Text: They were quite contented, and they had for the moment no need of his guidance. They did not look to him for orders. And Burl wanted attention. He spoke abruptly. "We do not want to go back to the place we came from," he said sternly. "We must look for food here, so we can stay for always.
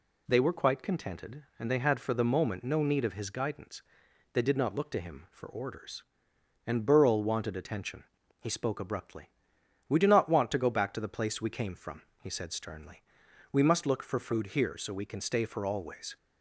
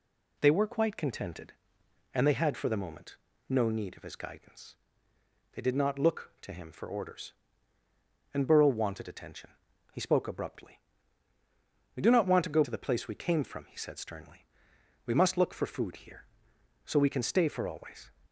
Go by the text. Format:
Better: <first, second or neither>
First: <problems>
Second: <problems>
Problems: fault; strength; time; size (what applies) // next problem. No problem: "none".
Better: first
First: none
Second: pauses between "moment" and "no"; slight; at 3.1 s; 0.32 s long // skips "back"; at 12.6 s